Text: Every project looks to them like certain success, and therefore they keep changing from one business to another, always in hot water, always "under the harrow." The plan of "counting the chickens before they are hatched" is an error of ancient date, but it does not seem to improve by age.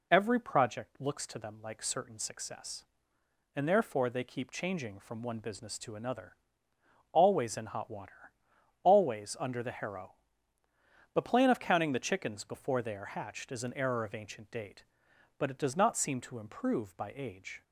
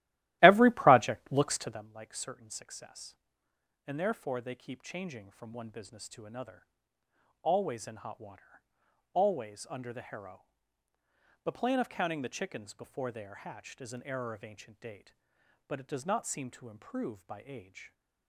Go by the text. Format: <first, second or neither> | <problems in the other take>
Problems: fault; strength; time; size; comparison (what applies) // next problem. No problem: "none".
first | starts louder than the rest; strong; until 1.9 s; 15.5 dB